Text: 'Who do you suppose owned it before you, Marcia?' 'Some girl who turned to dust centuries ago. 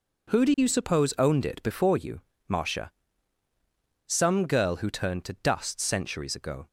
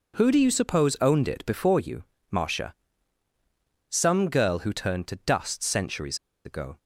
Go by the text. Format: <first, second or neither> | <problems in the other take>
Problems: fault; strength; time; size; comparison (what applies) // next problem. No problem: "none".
first | pauses between "centuries" and "ago"; slight; at 6.1 s; 0.28 s long